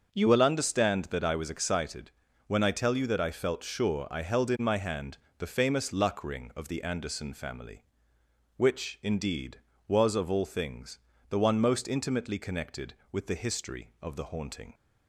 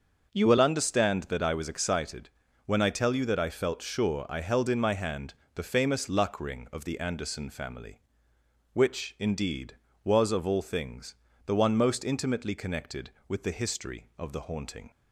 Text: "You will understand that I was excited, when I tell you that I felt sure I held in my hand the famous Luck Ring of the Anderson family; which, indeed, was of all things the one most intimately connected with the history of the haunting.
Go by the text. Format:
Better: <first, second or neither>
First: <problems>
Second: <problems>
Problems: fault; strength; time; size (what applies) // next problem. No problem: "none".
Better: neither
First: starts louder than the rest; until 1.1 s; 6.5 dB // pauses between "hand" and "the"; slight; at 5.1 s; 0.22 s long // pauses between "things" and "the"; slight; at 10.9 s; 0.32 s long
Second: starts louder than the rest; noticeable; until 1.4 s; 6 dB // pauses between "hand" and "the"; slight; at 5.3 s; 0.22 s long // pauses between "things" and "the"; slight; at 11.1 s; 0.32 s long